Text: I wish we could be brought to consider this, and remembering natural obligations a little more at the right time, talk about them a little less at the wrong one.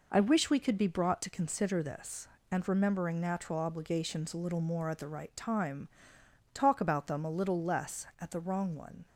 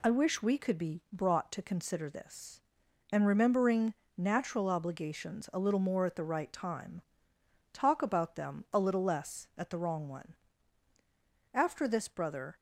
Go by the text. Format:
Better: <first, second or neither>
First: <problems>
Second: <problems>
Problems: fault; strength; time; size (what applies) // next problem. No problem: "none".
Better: first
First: none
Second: pauses between "remembering" and "natural"; slight; at 3.9 s; 0.24 s long // goes on to say "After this brother"; noticeable; from 11.5 s on; 1.0 s long